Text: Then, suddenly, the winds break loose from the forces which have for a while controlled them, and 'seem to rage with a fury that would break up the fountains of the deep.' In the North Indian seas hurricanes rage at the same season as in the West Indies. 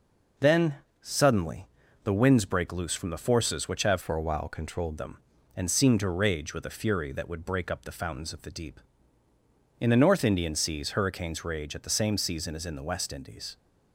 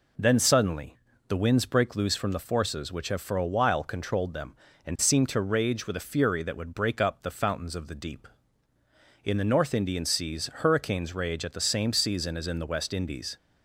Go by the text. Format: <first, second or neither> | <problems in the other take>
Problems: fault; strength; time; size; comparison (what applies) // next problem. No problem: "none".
second | changes voice from "for" to "controlled"; from 4.0 to 4.9 s; 0.9 s long